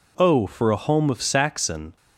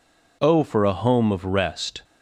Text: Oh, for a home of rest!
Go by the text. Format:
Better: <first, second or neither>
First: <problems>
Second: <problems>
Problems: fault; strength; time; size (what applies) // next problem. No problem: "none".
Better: second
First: says "saxon" for "rest"; at 1.2 s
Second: none